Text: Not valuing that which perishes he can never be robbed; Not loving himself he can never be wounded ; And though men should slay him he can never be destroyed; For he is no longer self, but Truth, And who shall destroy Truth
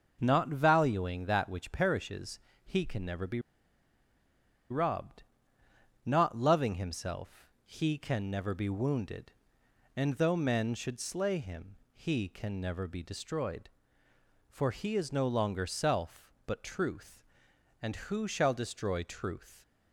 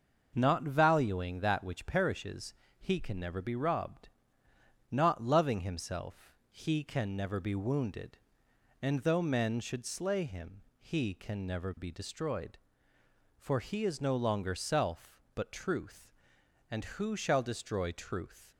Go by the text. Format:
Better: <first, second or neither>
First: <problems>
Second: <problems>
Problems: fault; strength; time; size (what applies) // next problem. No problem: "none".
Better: second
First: pauses between "perishes" and "he"; slight; at 2.3 s; 0.26 s long // pauses between "be" and "robbed"; strong; at 3.3 s; 1.3 s long // pauses between "himself" and "he"; slight; at 7.4 s; 0.16 s long // pauses between "him" and "he"; slight; at 11.7 s; 0.18 s long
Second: pauses between "perishes" and "he"; slight; at 2.5 s; 0.26 s long // pauses between "himself" and "he"; slight; at 6.3 s; 0.16 s long // pauses between "him" and "he"; slight; at 10.6 s; 0.18 s long